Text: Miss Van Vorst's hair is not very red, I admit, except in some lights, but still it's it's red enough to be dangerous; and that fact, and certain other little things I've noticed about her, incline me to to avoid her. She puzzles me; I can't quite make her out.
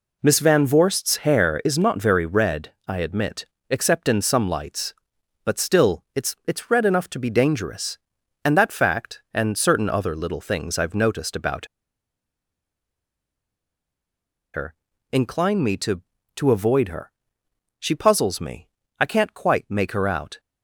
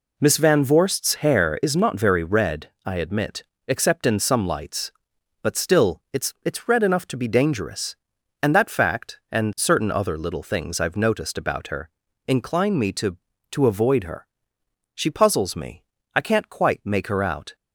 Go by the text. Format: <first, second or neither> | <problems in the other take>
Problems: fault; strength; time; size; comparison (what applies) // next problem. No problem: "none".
second | pauses between "about" and "her"; strong; at 11.6 s; 2.8 s long